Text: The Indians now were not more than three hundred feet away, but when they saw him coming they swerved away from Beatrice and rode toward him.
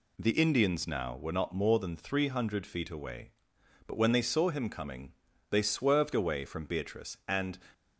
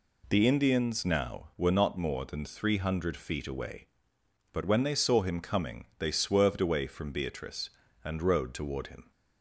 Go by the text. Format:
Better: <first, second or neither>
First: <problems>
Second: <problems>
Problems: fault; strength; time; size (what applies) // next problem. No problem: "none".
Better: second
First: pauses between "coming" and "they"; at 5.1 s; 0.38 s long // stops before "rode toward him"; at 7.7 s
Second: none